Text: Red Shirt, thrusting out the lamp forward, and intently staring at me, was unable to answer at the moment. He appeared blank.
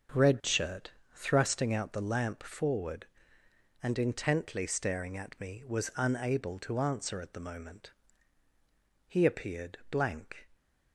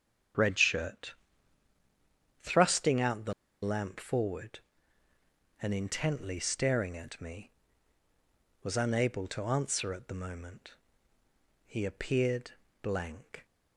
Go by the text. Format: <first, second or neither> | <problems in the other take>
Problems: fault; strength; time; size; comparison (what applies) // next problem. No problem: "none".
first | starts louder than the rest; strong; until 2.6 s; 8.5 dB; also in the first // pauses between "the" and "lamp"; slight; at 3.3 s; 0.29 s long // pauses between "appeared" and "blank"; slight; at 12.5 s; 0.28 s long